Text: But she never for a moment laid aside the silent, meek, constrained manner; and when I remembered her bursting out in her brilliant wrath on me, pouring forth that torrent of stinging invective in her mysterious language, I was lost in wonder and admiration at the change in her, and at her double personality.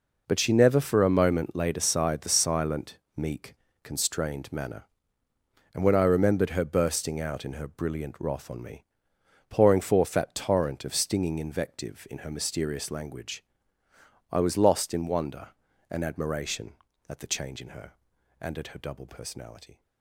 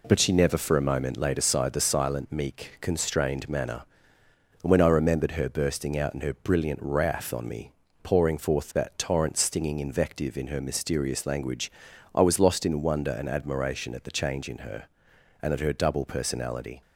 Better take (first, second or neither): first